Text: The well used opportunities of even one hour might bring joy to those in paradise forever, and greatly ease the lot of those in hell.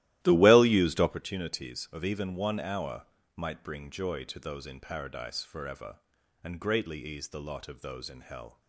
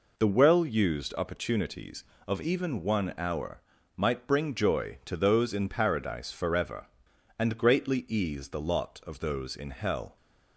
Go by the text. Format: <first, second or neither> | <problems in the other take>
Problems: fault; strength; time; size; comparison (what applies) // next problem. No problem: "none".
second | starts louder than the rest; strong; until 1.2 s; 15 dB // pauses between "hour" and "might"; slight; at 3.0 s; 0.28 s long; also in the second